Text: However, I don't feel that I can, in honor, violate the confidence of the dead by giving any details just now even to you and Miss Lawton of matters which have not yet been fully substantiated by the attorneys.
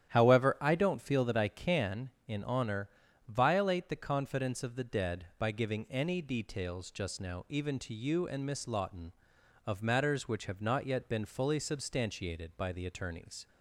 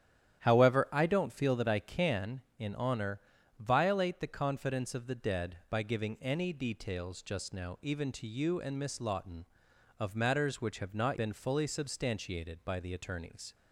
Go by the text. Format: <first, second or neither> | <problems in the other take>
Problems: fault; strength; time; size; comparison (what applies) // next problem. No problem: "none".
first | starts louder than the rest; strong; until 1.4 s; 10.5 dB; strong in the first // skips "yet"; at 11.1 s